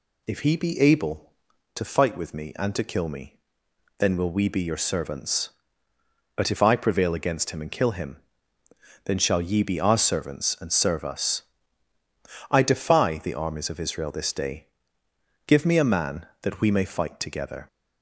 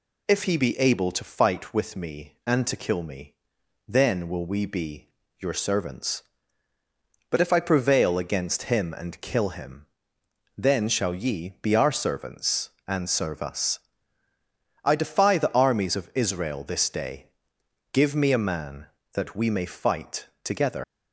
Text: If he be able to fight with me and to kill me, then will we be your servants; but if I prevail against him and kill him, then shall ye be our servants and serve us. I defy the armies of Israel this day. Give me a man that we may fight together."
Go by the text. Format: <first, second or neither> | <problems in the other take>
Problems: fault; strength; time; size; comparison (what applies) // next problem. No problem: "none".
first | pauses between "be" and "your"; slight; at 5.0 s; 0.30 s long // pauses between "fight" and "together"; slight; at 20.2 s; 0.18 s long // leaves "together" unfinished; at 20.8 s; 145 ms